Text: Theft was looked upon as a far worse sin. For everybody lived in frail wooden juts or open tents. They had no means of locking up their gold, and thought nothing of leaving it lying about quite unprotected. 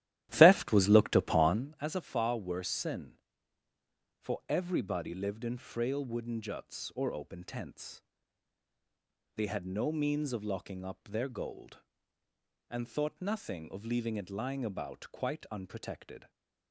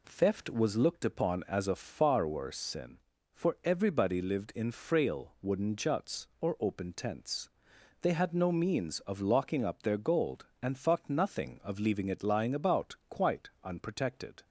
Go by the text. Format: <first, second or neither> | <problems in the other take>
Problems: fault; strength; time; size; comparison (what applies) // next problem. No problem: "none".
second | starts louder than the rest; strong; until 1.7 s; 13.5 dB